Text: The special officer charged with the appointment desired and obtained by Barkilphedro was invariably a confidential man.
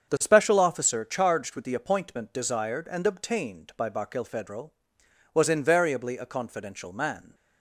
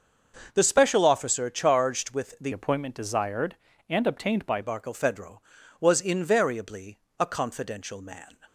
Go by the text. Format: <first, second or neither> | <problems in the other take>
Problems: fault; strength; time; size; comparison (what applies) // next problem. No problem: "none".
first | starts louder than the rest; until 1.5 s; 6 dB; strong in the first // changes voice from "appointment" to "by"; from 2.5 to 4.6 s; 2.1 s long // pauses between "invariably" and "a"; slight; at 6.9 s; 0.22 s long